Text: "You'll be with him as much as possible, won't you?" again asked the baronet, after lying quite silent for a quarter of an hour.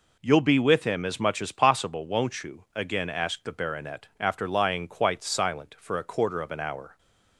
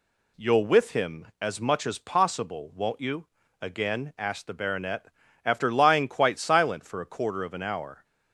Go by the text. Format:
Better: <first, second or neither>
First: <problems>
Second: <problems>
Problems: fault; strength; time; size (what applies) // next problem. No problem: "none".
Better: first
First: none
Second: skips "be"; at 0.6 s